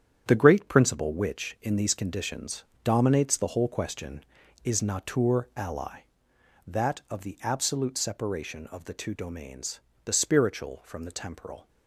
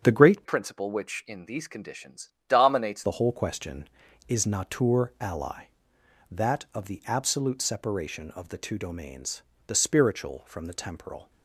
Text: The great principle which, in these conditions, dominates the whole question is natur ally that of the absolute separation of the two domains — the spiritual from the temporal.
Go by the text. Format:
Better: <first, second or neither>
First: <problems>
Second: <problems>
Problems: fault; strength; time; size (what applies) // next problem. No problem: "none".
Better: first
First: starts louder than the rest; strong; until 1.2 s; 9 dB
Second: starts louder than the rest; strong; until 1.0 s; 7.5 dB // changes voice from "principle" to "dominates"; from 0.4 to 3.0 s; 2.6 s long